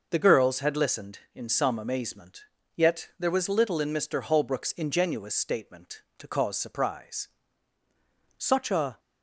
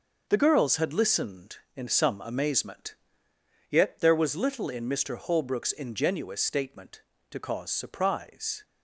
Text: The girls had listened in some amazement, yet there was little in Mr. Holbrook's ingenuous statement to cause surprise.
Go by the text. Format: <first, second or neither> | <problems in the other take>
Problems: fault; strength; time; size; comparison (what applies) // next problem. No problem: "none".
second | goes on to say "Such a"; from 8.3 s on; 0.60 s long